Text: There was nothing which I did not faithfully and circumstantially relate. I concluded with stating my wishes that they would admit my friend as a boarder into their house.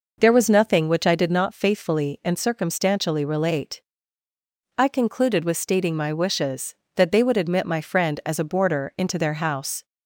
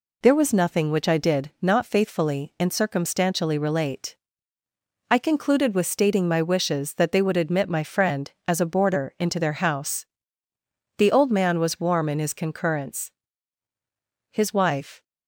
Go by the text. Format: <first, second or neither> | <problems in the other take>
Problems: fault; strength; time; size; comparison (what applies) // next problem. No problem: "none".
first | goes on to say "The old man was warm in his concurrence His wife"; strong; from 10.9 s on; 4.0 s long